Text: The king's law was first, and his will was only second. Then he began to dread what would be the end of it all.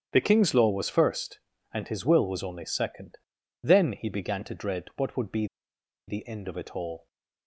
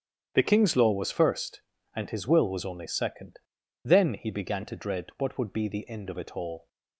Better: second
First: starts louder than the rest; strong; until 1.1 s; 9 dB // pauses between "be" and "the"; noticeable; at 5.4 s; 0.62 s long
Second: starts louder than the rest; strong; until 1.3 s; 9 dB

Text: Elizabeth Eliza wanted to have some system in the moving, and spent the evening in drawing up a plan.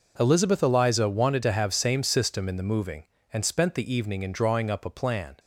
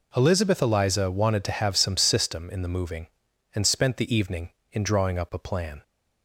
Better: second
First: says "same" for "some"; at 1.7 s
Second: none

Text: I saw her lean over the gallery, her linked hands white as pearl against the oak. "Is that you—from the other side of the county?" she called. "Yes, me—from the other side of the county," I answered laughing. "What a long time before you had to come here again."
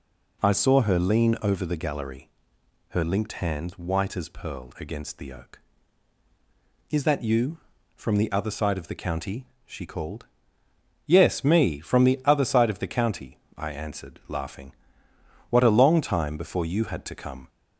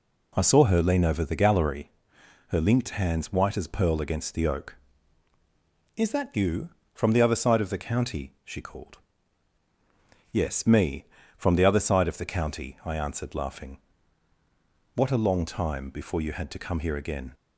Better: second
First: stops before "here again"; at 17.4 s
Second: none

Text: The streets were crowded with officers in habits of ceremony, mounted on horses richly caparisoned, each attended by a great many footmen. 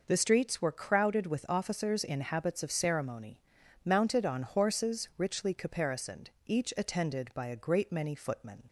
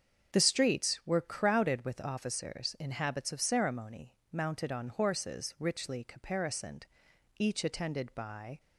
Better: first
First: none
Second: starts louder than the rest; until 1.4 s; 7 dB // stops before "a great many footmen"; at 8.5 s

